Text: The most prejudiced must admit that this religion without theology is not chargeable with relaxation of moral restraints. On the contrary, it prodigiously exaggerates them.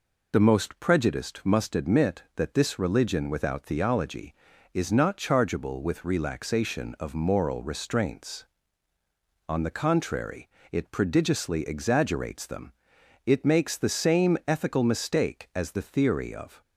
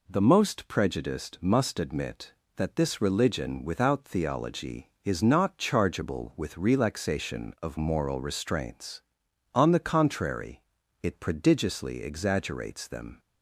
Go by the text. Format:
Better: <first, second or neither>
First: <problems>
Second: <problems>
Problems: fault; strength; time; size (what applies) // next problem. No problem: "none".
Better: second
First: goes on to say "It makes the same ethical mistake as the theory of"; strong; from 13.2 s on; 3.3 s long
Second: none